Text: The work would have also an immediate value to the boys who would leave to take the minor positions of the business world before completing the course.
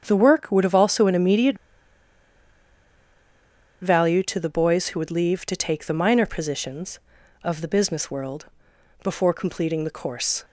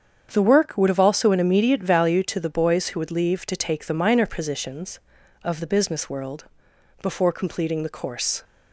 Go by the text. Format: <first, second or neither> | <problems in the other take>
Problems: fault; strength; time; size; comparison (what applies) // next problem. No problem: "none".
second | starts louder than the rest; strong; until 1.0 s; 7.5 dB; strong in the second // pauses between "immediate" and "value"; strong; at 1.5 s; 2.2 s long // pauses between "world" and "before"; noticeable; at 8.4 s; 0.58 s long; noticeable in the second